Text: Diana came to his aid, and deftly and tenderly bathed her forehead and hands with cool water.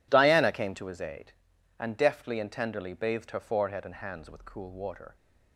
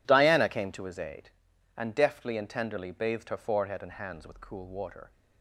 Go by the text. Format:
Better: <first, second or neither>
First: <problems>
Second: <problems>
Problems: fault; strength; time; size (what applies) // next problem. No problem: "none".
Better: neither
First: none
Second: none